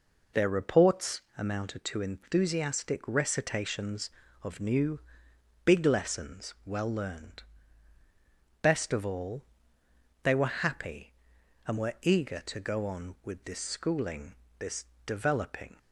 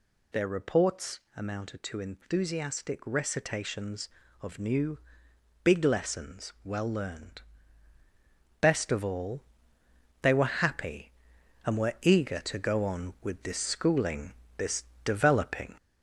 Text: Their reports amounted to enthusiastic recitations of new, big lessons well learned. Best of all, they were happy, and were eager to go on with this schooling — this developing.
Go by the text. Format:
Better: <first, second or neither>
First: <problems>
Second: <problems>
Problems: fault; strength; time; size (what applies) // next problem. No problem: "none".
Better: first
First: pauses between "reports" and "amounted"; slight; at 1.2 s; 0.16 s long // pauses between "this" and "developing"; slight; at 14.8 s; 0.20 s long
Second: gets louder; noticeable; throughout; 4 dB // pauses between "reports" and "amounted"; slight; at 1.1 s; 0.16 s long // pauses between "this" and "developing"; slight; at 14.8 s; 0.20 s long